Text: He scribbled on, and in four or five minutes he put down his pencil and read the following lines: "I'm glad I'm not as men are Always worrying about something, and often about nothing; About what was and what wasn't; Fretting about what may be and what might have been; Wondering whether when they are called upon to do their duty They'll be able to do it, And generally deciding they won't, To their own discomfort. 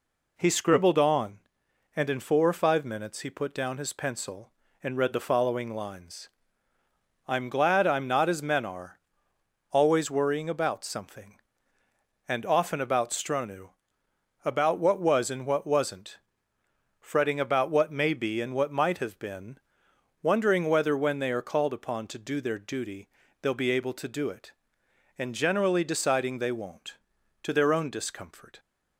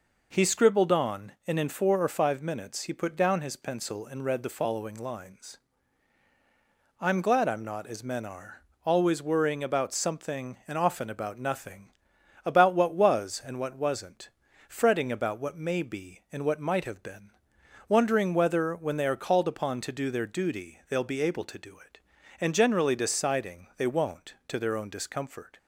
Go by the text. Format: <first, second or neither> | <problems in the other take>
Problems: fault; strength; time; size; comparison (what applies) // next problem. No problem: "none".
second | pauses between "are" and "Always"; noticeable; at 8.9 s; 0.72 s long; slight in the second // says "stronu" for "nothing"; at 13.0 s // pauses between "duty" and "They'll"; slight; at 23.0 s; 0.34 s long